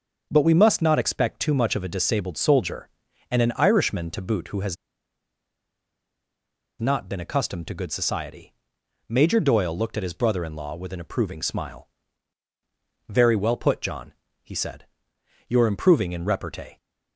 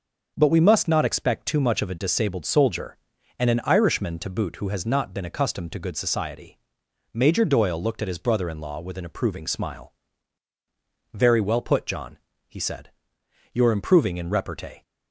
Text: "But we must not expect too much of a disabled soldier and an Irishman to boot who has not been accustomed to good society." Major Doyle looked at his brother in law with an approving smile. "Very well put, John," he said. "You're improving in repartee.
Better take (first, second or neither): second